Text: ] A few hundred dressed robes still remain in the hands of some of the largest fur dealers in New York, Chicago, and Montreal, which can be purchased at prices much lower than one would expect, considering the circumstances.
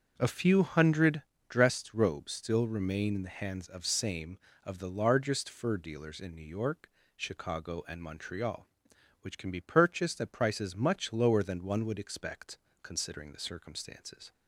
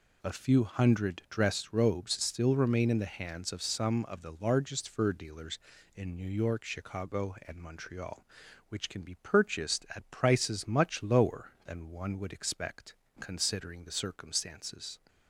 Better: second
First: starts louder than the rest; until 1.1 s; 7 dB // pauses between "hundred" and "dressed"; slight; at 1.2 s; 0.26 s long // says "same" for "some"; at 3.8 s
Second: none

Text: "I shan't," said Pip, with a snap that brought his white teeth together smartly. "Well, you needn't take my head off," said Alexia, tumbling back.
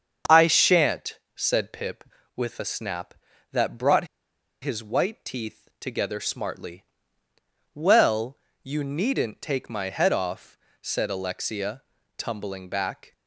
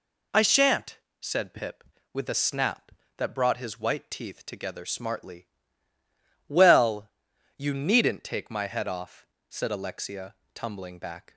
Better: second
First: starts louder than the rest; strong; until 1.4 s; 7 dB // pauses between "brought" and "his"; noticeable; at 4.0 s; 0.57 s long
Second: none

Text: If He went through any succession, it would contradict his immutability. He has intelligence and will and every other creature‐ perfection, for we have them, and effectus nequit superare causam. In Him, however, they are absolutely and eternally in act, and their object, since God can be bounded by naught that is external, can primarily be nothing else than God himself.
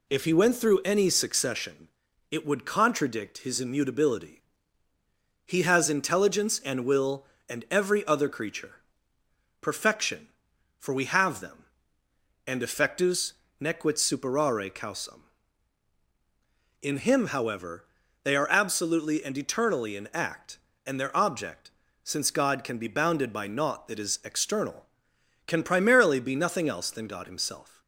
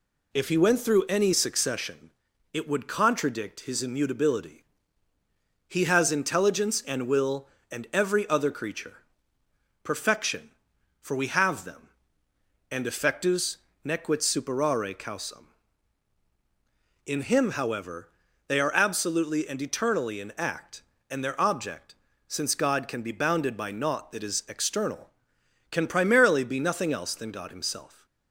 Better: neither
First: pauses between "effectus" and "nequit"; slight; at 13.3 s; 0.26 s long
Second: pauses between "effectus" and "nequit"; slight; at 13.5 s; 0.26 s long

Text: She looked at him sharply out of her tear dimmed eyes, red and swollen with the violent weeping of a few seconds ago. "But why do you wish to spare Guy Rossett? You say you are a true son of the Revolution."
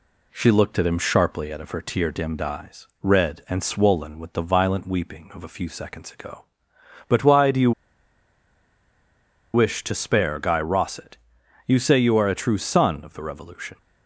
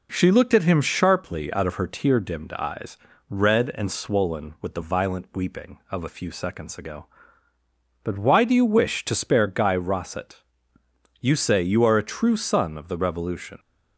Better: second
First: pauses between "you" and "wish"; strong; at 7.7 s; 1.8 s long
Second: none

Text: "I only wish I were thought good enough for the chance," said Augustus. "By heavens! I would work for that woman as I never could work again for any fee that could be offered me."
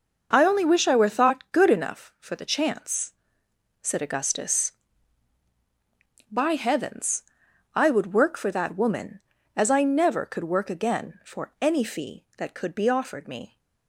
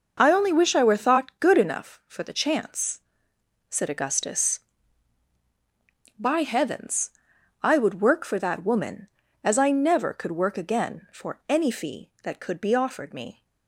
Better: neither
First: none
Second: none

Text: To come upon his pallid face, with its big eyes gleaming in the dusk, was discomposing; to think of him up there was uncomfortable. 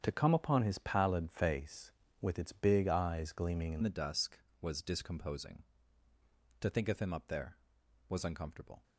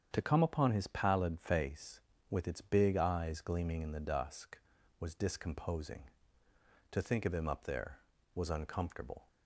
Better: second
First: starts louder than the rest; strong; until 1.0 s; 8 dB // changes voice at "the"; from 3.8 s on; 5.0 s long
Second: starts louder than the rest; strong; until 1.1 s; 8 dB

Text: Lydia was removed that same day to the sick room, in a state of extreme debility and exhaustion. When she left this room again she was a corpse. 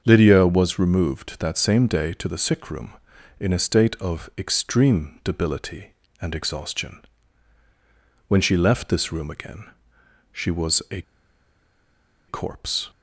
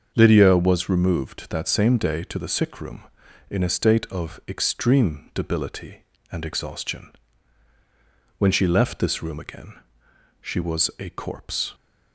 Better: second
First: starts louder than the rest; until 1.0 s; 7 dB // pauses between "again" and "she"; noticeable; at 9.6 s; 0.68 s long // pauses between "a" and "corpse"; strong; at 11.0 s; 1.2 s long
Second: starts louder than the rest; until 1.1 s; 7 dB // pauses between "again" and "she"; noticeable; at 9.7 s; 0.68 s long

